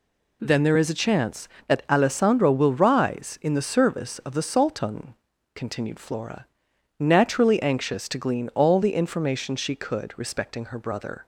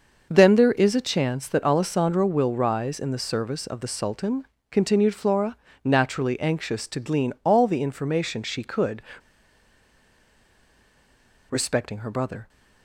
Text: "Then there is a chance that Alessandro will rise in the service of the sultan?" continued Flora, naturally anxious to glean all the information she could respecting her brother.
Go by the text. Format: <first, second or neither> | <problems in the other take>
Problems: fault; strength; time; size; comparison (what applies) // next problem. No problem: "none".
first | pauses between "could" and "respecting"; strong; at 9.0 s; 2.4 s long